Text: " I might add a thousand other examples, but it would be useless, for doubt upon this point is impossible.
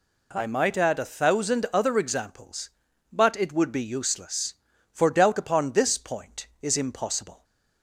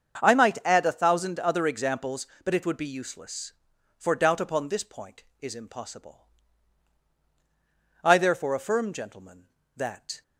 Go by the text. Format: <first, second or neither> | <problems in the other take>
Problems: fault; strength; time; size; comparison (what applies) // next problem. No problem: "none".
first | starts louder than the rest; until 1.2 s; 7 dB // goes on to say "I therefore affirm gentlemen that"; strong; from 8.0 s on; 2.2 s long